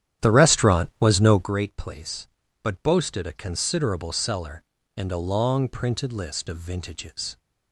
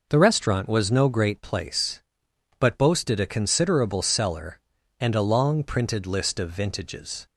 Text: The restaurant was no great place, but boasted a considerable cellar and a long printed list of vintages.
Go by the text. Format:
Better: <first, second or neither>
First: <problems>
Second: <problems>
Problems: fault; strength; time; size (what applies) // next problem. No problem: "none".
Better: second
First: starts louder than the rest; strong; until 1.5 s; 10.5 dB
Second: none